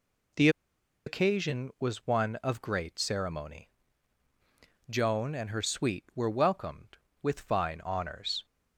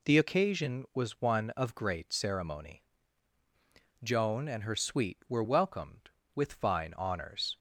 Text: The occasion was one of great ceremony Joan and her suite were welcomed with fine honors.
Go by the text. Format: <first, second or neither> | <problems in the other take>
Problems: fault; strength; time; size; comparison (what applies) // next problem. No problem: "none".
second | pauses between "The" and "occasion"; noticeable; at 0.4 s; 0.57 s long // pauses between "ceremony" and "Joan"; at 3.6 s; 1.2 s long; also in the second